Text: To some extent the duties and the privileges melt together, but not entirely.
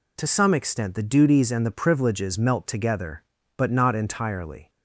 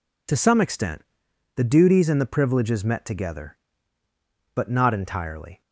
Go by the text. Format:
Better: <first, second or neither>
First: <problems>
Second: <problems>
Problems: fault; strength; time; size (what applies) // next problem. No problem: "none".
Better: first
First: none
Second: pauses between "extent" and "the"; noticeable; at 1.0 s; 0.54 s long // says "met" for "melt"; at 2.8 s